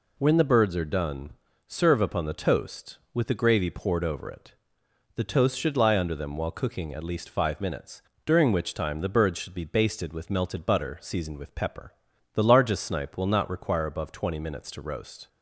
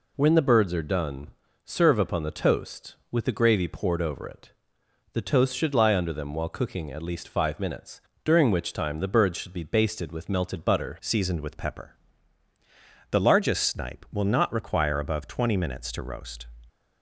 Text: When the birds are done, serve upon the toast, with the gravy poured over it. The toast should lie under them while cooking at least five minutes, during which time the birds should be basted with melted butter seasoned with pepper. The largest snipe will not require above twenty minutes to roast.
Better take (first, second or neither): first